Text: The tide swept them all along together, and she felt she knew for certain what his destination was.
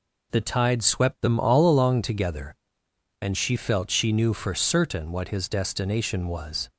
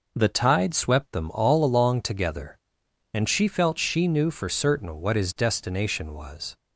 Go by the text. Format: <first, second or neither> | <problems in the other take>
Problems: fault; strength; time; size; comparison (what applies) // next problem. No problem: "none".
neither | none